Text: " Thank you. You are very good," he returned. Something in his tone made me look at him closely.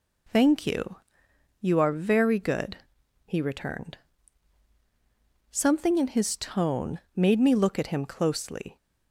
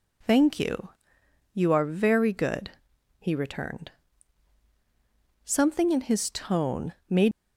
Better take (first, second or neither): first